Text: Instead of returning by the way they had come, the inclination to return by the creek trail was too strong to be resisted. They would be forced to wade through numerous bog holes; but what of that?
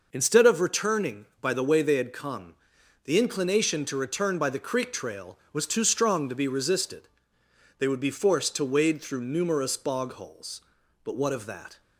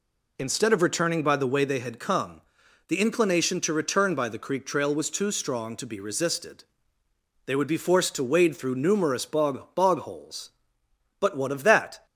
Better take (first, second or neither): first